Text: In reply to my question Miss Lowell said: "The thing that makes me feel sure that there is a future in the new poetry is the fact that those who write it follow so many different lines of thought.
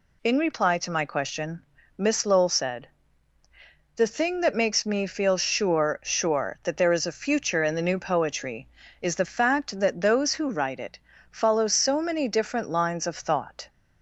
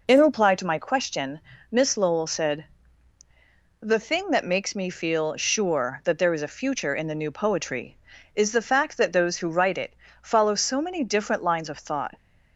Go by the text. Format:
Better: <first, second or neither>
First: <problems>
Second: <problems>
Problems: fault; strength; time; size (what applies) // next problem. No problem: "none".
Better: second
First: pauses between "question" and "Miss"; slight; at 1.6 s; 0.32 s long // says "sure" twice; at 6.0 s // pauses between "it" and "follow"; slight; at 10.9 s; 0.32 s long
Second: pauses between "question" and "Miss"; slight; at 1.4 s; 0.30 s long // pauses between "it" and "follow"; slight; at 9.9 s; 0.26 s long